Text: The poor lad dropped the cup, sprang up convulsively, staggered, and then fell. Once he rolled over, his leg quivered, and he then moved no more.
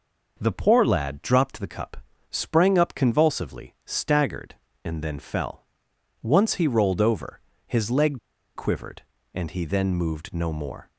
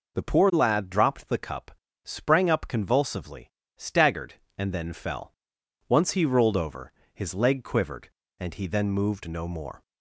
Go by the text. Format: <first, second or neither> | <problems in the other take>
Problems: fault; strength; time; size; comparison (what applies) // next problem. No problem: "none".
second | pauses between "leg" and "quivered"; at 8.1 s; 0.36 s long